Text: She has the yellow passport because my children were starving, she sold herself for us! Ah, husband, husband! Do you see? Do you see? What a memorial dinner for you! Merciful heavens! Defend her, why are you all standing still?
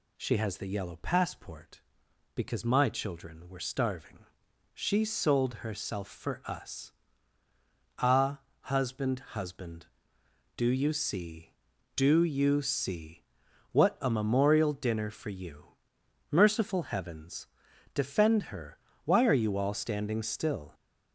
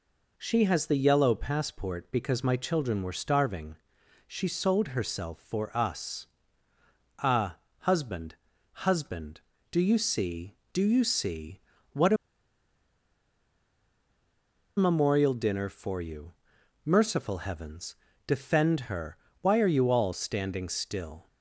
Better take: first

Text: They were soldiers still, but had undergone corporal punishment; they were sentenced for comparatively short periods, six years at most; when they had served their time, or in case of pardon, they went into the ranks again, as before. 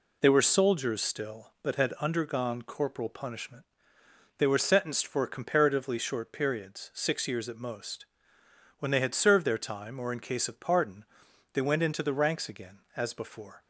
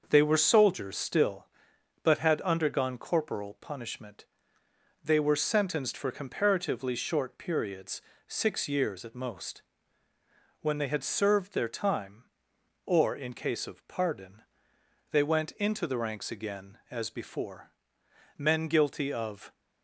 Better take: first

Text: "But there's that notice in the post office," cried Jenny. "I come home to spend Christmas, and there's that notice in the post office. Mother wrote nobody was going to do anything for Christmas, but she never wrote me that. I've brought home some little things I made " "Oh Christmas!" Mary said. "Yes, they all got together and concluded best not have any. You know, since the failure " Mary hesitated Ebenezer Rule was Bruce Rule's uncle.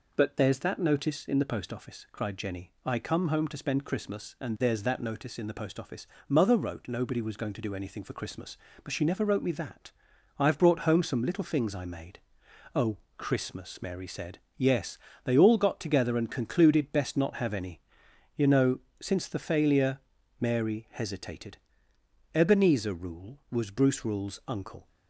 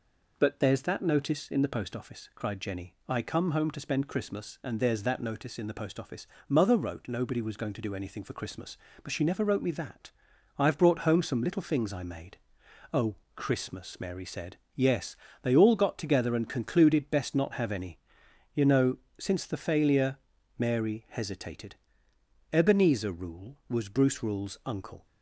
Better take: neither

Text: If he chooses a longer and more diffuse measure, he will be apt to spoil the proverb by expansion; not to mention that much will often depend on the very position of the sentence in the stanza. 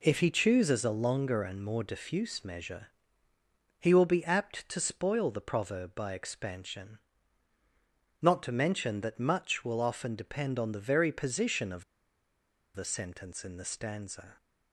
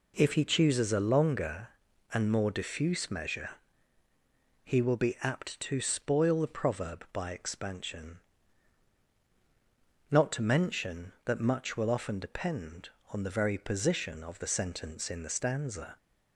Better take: second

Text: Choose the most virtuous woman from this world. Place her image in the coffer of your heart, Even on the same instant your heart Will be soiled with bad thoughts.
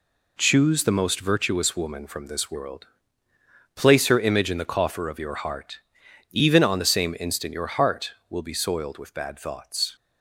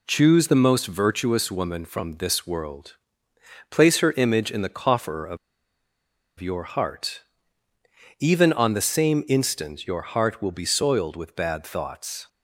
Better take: first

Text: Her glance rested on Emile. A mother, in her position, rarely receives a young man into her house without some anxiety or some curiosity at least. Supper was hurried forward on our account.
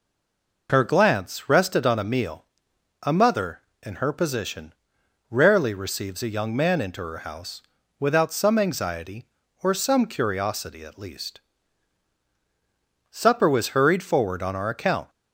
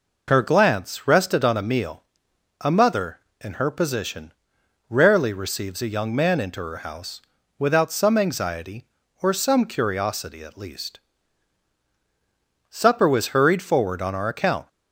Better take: second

